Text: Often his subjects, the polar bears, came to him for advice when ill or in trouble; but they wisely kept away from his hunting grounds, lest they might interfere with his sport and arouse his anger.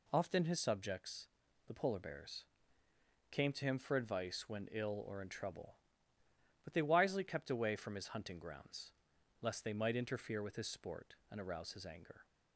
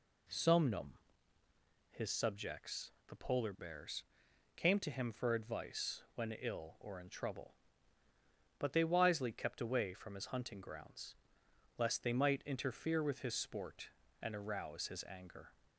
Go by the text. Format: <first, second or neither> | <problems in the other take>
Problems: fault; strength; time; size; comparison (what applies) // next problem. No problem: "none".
first | says "Somnum" for "Often"; at 0.2 s